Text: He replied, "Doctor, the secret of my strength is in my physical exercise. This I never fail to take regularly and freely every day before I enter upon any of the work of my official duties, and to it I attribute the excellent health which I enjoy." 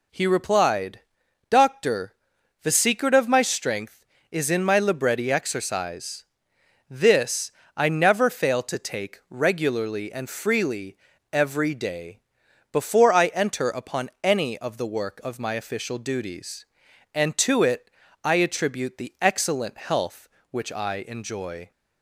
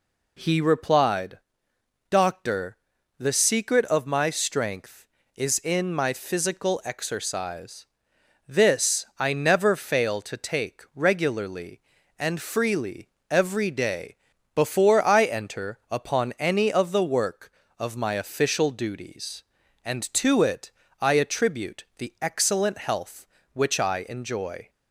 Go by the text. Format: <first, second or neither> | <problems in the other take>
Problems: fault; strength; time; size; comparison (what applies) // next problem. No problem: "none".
second | says "libretti" for "physical"; at 4.7 s // pauses between "This" and "I"; slight; at 7.5 s; 0.26 s long // pauses between "freely" and "every"; slight; at 10.9 s; 0.34 s long; slight in the second // pauses between "day" and "before"; noticeable; at 12.1 s; 0.54 s long; also in the second // pauses between "it" and "I"; slight; at 17.8 s; 0.34 s long; slight in the second